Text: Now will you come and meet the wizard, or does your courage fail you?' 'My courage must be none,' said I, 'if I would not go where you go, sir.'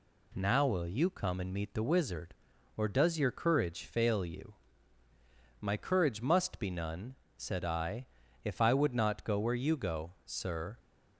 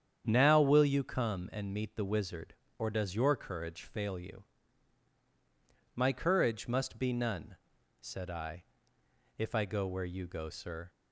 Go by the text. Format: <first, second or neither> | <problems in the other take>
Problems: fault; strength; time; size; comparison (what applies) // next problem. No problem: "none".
first | starts louder than the rest; strong; until 1.2 s; 8.5 dB // skips "would not"; at 9.6 s